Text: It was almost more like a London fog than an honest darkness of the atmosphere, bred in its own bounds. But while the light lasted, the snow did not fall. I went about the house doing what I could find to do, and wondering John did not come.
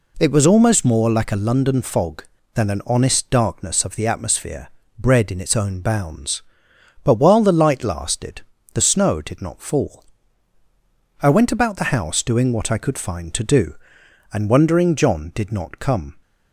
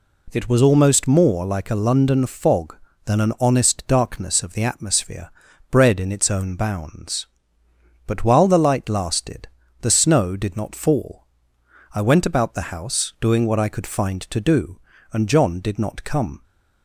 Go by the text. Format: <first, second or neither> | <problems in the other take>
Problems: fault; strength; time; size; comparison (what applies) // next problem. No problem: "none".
first | skips "wondering"; at 15.2 s